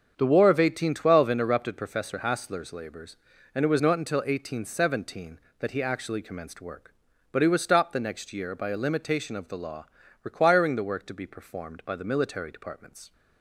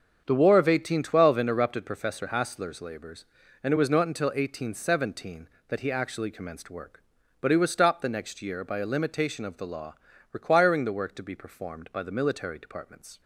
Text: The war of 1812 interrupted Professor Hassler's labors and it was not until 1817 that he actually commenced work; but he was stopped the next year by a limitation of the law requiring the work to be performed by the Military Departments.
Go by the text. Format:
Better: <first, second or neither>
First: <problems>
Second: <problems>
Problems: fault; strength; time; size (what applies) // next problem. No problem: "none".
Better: neither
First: starts louder than the rest; until 1.1 s; 7 dB // pauses between "law" and "requiring"; slight; at 9.8 s; 0.34 s long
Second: starts louder than the rest; until 1.2 s; 7 dB // pauses between "law" and "requiring"; slight; at 9.9 s; 0.34 s long